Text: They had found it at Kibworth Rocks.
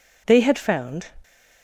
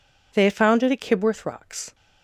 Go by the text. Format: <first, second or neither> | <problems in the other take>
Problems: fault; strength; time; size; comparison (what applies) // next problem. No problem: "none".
second | stops before "it at Kibworth Rocks"; at 1.2 s